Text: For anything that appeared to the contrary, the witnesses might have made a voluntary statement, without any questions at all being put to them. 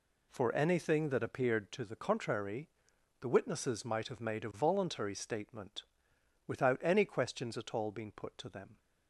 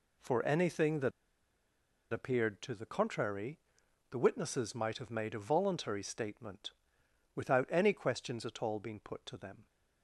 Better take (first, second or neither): first